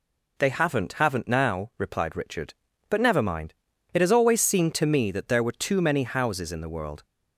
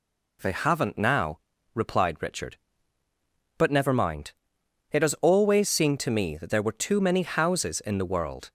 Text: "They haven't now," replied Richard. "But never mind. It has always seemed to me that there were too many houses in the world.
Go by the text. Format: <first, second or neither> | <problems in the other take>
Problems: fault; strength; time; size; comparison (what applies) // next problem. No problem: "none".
second | says "haven't" twice; at 0.9 s